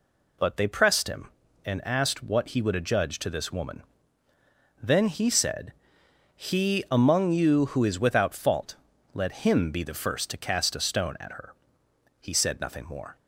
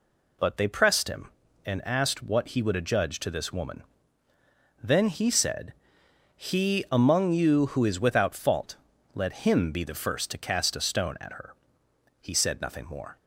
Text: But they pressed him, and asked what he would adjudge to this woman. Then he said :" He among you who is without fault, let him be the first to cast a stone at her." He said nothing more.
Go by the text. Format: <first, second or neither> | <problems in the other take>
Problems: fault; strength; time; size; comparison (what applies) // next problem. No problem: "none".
neither | none